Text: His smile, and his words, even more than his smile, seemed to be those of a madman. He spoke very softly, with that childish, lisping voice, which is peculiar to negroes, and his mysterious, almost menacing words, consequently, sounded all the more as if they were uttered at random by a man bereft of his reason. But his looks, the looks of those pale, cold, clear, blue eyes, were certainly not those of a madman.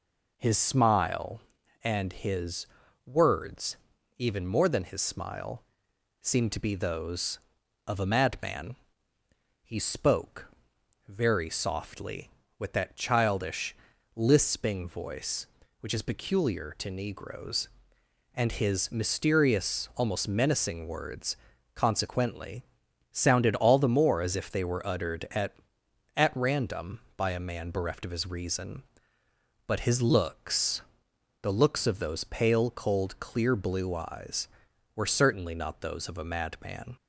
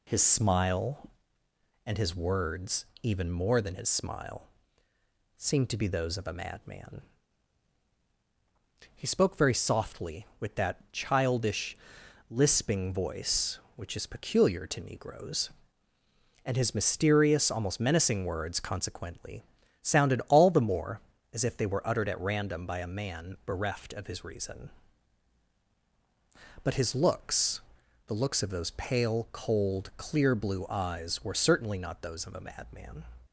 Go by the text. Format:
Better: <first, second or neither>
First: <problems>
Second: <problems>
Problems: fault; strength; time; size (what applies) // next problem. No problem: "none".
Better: second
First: pauses between "his" and "words"; at 2.6 s; 0.38 s long // pauses between "spoke" and "very"; noticeable; at 10.4 s; 0.60 s long // says "at" twice; at 26.1 s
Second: none